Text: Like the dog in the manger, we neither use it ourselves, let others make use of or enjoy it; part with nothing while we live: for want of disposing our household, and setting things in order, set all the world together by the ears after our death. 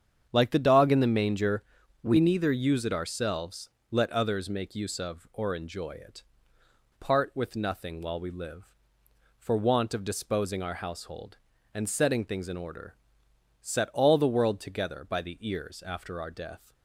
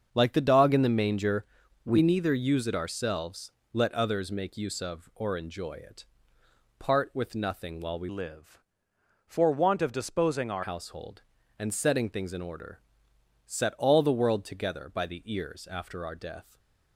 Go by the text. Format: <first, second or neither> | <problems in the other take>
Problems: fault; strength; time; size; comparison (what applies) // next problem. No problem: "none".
first | starts louder than the rest; until 1.1 s; 7 dB; strong in the first // changes voice from "live" to "our"; from 8.0 to 10.6 s; 2.6 s long // stays silent after the last word; slight; from 16.4 s on; 0.5 s long